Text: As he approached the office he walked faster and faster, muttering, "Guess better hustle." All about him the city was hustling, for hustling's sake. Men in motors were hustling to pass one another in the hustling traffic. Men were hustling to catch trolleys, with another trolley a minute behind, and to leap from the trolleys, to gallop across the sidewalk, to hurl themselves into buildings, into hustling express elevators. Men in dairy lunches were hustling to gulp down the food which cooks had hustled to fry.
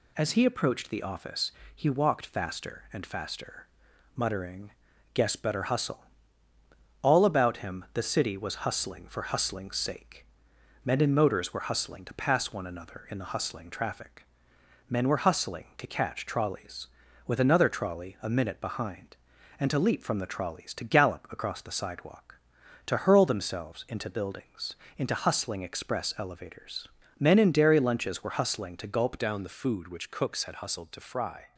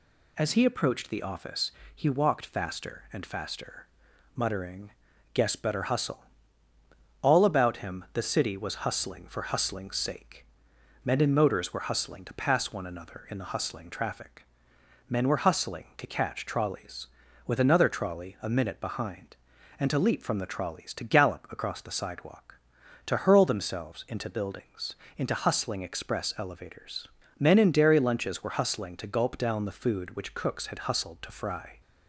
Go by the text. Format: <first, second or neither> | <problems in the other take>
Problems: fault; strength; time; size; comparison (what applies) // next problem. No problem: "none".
second | pauses between "office" and "he"; slight; at 1.5 s; 0.24 s long; slight in the second // changes voice at "down"; from 29.1 s on; 2.4 s long